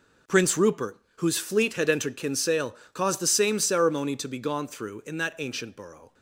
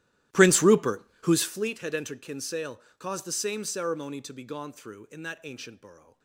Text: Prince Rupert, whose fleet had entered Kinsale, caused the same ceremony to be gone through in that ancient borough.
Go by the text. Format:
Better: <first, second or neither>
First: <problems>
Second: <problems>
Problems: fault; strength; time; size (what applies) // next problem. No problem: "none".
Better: first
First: none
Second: starts louder than the rest; strong; until 1.7 s; 14.5 dB